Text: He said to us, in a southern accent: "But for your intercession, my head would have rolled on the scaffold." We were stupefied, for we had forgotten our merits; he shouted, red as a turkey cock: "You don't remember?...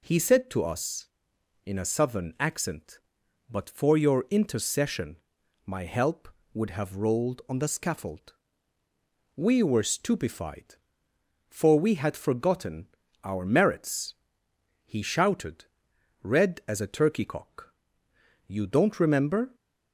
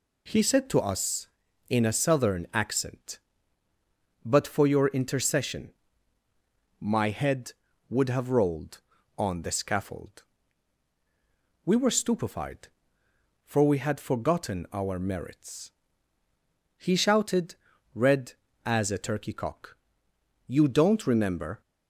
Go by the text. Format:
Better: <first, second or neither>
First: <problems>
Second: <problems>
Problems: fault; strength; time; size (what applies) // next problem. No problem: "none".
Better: second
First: says "help" for "head"; at 5.8 s // pauses between "forgotten" and "our"; slight; at 12.8 s; 0.36 s long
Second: none